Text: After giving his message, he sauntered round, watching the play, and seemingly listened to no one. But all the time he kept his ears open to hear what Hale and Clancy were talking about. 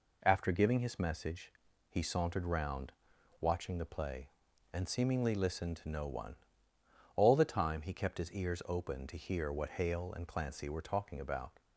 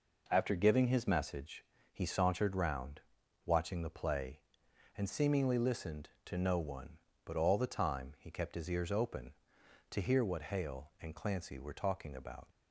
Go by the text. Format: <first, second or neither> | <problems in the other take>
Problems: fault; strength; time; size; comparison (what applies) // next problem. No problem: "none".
second | skips "But"; at 6.7 s